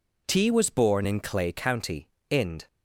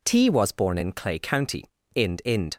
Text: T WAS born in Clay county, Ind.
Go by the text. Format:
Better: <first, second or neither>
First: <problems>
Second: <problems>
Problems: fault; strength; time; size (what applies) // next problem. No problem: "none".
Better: first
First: none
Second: says "Ind" twice; at 2.2 s